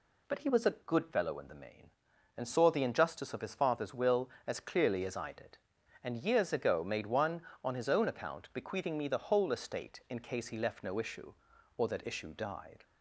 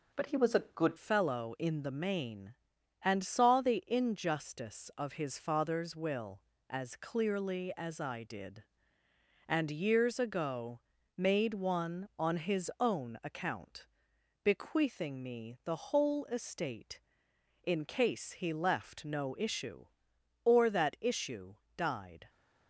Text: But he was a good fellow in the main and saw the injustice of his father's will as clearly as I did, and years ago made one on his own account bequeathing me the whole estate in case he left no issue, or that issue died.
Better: first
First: none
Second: changes voice at "fellow"; from 0.9 s on; 21.3 s long // pauses between "ago" and "made"; slight; at 10.8 s; 0.36 s long // pauses between "account" and "bequeathing"; noticeable; at 13.8 s; 0.56 s long // pauses between "issue" and "died"; slight; at 21.5 s; 0.20 s long

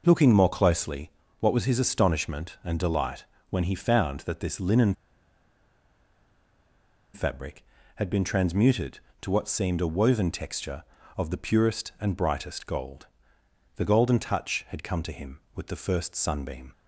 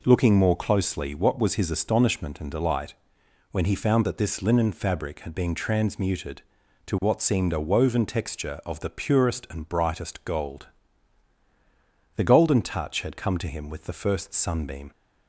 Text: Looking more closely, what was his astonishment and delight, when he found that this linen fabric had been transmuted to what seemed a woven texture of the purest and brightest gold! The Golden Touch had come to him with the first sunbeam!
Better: second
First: pauses between "linen" and "fabric"; strong; at 4.9 s; 2.2 s long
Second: none

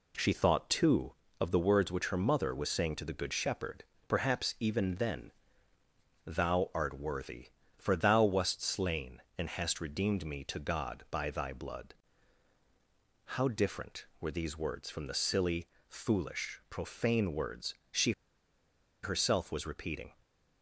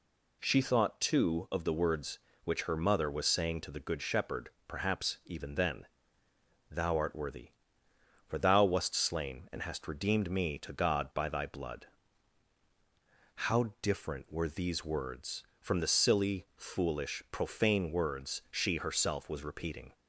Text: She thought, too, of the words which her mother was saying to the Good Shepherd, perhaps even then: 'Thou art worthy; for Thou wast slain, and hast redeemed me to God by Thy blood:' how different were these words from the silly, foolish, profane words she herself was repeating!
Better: second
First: pauses between "words" and "she"; slight; at 17.7 s; 0.16 s long // pauses between "she" and "herself"; noticeable; at 18.1 s; 0.91 s long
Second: none

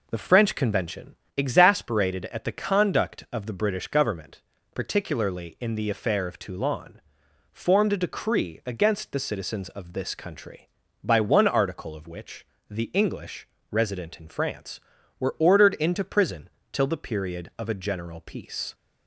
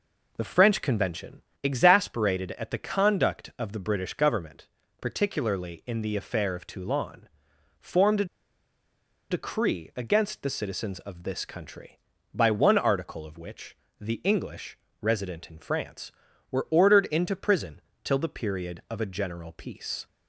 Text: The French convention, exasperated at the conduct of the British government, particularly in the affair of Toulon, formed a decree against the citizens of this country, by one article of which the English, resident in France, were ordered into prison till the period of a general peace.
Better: first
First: pauses between "which" and "the"; slight; at 12.4 s; 0.24 s long // pauses between "prison" and "till"; slight; at 16.4 s; 0.24 s long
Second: pauses between "a" and "decree"; at 8.2 s; 1.0 s long // pauses between "which" and "the"; slight; at 13.7 s; 0.24 s long // pauses between "prison" and "till"; slight; at 17.8 s; 0.24 s long

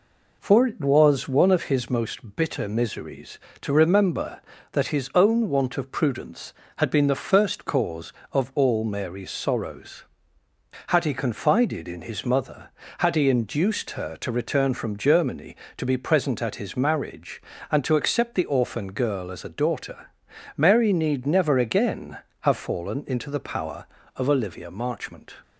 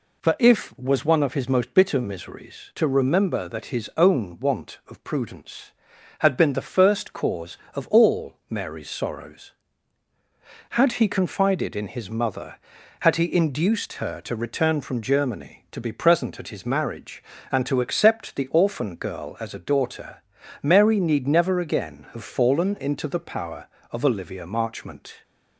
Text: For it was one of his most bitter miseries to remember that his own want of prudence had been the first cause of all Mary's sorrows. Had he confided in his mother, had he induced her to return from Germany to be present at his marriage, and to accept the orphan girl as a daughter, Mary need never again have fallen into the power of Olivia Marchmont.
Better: first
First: none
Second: says "if" for "it"; at 0.3 s // pauses between "all" and "Mary's"; slight; at 8.3 s; 0.16 s long

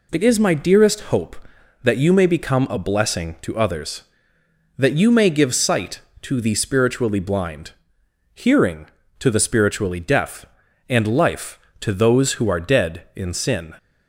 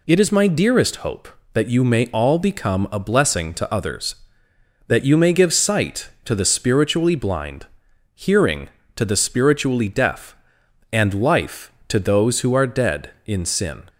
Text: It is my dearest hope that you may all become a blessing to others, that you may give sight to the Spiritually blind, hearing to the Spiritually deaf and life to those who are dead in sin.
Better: second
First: skips "all"; at 2.2 s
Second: none

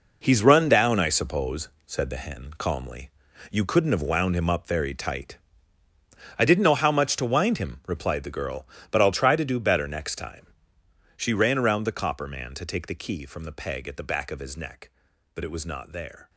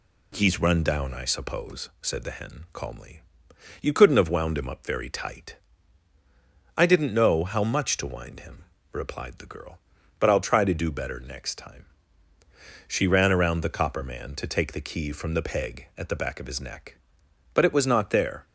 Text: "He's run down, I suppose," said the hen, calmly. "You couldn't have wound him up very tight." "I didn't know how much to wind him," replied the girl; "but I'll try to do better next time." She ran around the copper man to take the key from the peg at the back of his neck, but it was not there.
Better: second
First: gets quieter; strong; throughout; 10.5 dB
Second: none

